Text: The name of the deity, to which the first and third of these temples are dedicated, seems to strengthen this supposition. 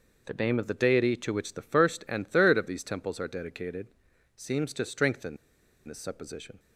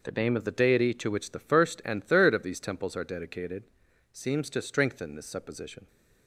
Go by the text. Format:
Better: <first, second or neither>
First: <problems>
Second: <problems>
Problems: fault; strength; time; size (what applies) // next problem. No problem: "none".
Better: second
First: pauses between "strengthen" and "this"; noticeable; at 5.3 s; 0.50 s long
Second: none